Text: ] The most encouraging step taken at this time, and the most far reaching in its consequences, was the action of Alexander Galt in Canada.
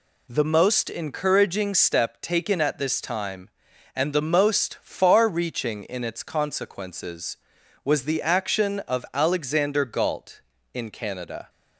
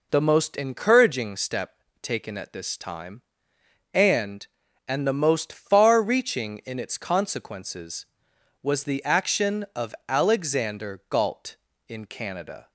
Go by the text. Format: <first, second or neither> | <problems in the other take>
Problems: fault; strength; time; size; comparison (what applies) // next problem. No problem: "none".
first | pauses between "step" and "taken"; slight; at 1.7 s; 0.26 s long // says "and" twice; at 4.8 s // pauses between "of" and "Alexander"; slight; at 9.9 s; 0.16 s long